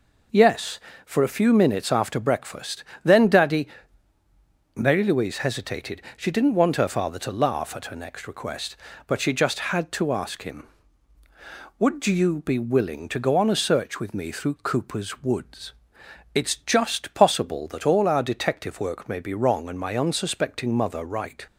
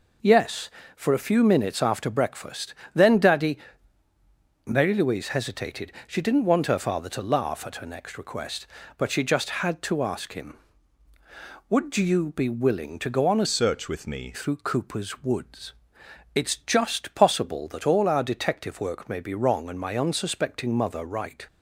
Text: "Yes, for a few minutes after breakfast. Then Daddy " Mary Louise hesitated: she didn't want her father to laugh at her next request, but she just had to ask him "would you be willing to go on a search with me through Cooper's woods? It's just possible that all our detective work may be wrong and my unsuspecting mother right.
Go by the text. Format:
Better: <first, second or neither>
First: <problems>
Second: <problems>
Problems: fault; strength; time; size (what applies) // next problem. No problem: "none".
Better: first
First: none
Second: changes voice from "search" to "me"; from 13.4 to 14.3 s; 0.9 s long